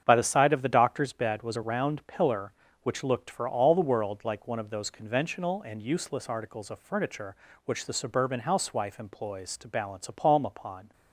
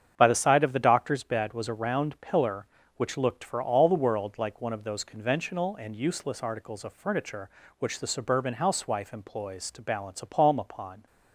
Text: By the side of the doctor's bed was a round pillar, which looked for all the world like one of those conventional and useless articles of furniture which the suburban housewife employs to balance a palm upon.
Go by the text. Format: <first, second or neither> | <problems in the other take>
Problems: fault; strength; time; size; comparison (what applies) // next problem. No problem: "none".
neither | starts louder than the rest; strong; the same in both